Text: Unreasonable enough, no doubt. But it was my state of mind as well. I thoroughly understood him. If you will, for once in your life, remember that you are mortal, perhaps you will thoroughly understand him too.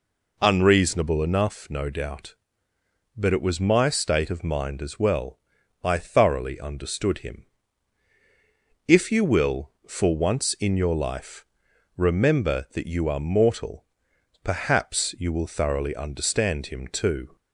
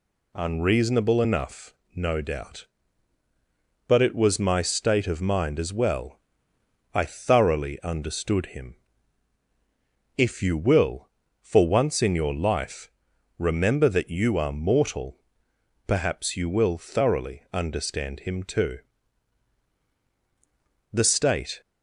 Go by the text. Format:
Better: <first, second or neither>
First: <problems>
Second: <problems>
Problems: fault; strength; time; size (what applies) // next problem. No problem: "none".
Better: first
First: none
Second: goes on to say "The state"; noticeable; from 20.9 s on; 0.68 s long